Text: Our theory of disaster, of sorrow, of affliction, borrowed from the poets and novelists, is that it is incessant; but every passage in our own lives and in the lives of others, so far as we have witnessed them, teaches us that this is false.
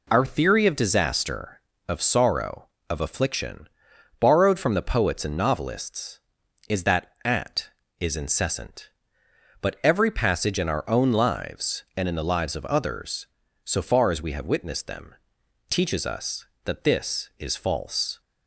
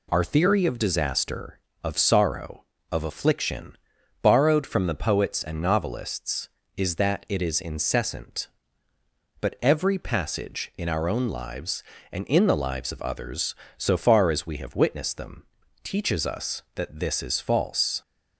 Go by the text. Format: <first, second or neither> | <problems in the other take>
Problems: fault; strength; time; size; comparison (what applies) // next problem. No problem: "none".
second | says "at" for "it"; at 7.2 s